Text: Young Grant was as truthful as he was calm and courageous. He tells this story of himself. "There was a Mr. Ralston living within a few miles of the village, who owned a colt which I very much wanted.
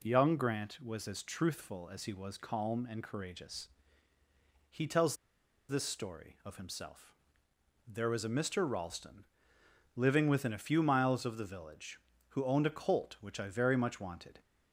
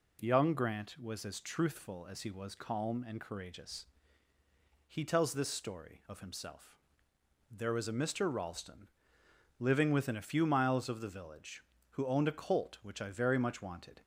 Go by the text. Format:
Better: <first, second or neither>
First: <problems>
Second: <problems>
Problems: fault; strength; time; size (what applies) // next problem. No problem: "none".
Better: second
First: pauses between "tells" and "this"; noticeable; at 5.1 s; 0.52 s long // pauses between "Ralston" and "living"; noticeable; at 9.2 s; 0.72 s long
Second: pauses between "Ralston" and "living"; noticeable; at 8.8 s; 0.72 s long